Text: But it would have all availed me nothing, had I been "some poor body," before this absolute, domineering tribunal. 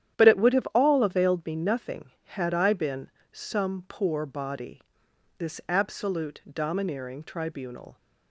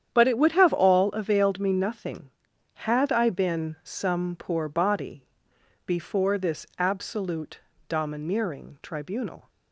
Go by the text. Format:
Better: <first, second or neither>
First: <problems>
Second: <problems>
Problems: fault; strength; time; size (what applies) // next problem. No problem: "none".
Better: second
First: starts louder than the rest; strong; until 1.2 s; 9.5 dB // pauses between "been" and "some"; slight; at 3.0 s; 0.22 s long // skips "before"; at 5.0 s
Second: starts louder than the rest; strong; until 1.1 s; 9.5 dB